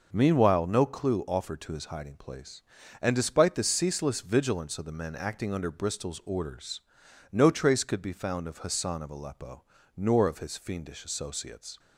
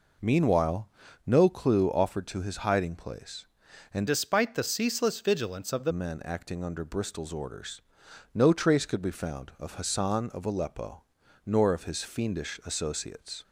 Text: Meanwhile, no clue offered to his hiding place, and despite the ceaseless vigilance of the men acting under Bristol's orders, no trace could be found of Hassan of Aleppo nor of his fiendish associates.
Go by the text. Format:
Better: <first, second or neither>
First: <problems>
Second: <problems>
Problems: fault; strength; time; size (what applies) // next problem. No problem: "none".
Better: first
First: pauses between "Aleppo" and "nor"; slight; at 9.6 s; 0.36 s long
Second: changes voice from "despite" to "the"; from 4.0 to 5.9 s; 1.9 s long // pauses between "Aleppo" and "nor"; at 11.0 s; 0.40 s long